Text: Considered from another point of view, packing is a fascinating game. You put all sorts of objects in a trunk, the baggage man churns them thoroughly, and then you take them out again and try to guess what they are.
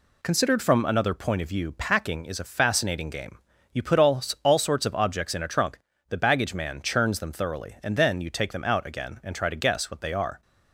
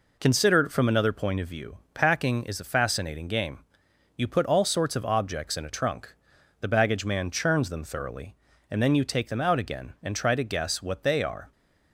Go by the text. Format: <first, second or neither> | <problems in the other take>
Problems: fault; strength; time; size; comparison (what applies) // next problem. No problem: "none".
second | says "all" twice; at 4.4 s